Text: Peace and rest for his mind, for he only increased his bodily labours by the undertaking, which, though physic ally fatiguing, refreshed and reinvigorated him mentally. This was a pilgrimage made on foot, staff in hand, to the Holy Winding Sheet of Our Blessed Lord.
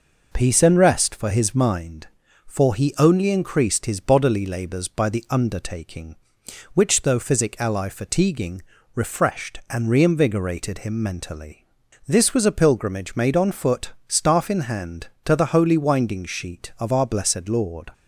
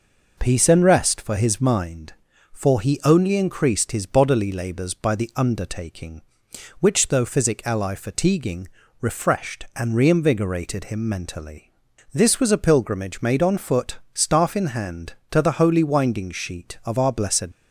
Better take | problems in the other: first | stops before "Lord"; at 17.5 s

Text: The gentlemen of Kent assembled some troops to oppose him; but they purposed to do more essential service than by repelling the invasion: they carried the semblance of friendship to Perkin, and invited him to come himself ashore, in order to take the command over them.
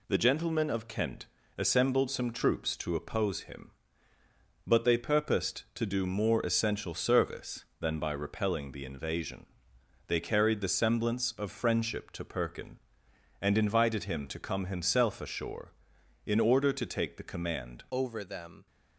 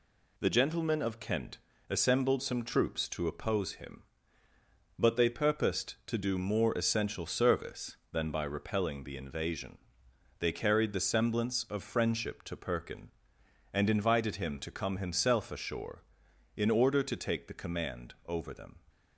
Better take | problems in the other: second | pauses between "Kent" and "assembled"; slight; at 1.2 s; 0.32 s long; slight in the second // changes voice at "over"; from 17.8 s on; 0.8 s long

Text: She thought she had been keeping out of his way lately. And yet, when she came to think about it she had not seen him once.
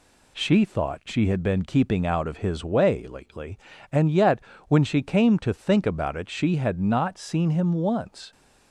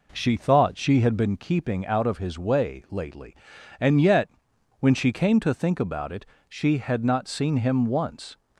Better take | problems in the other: first | starts louder than the rest; noticeable; until 1.4 s; 4 dB // pauses between "it" and "she"; slight; at 6.2 s; 0.22 s long

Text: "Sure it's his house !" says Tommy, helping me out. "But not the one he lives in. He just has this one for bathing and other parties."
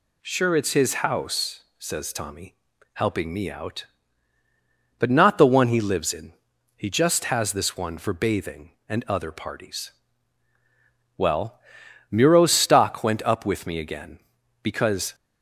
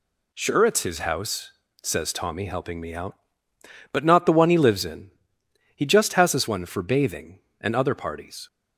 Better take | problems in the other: second | goes on to say "Well Muro's stock went up with me again because"; strong; from 11.1 s on; 3.9 s long

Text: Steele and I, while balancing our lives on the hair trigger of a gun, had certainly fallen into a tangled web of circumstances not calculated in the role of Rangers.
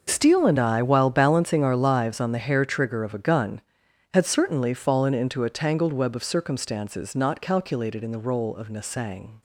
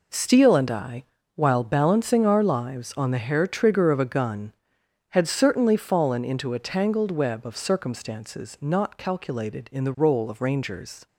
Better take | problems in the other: second | says "Nasang" for "Rangers"; at 8.6 s

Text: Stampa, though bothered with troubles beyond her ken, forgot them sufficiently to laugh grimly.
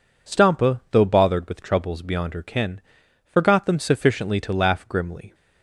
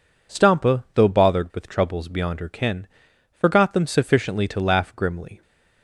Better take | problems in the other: neither | none

